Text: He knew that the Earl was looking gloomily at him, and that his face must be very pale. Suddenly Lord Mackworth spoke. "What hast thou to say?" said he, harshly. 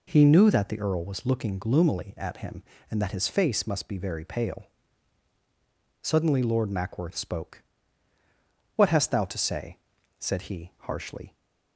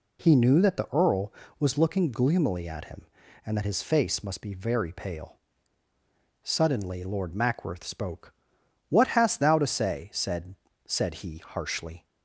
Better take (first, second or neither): first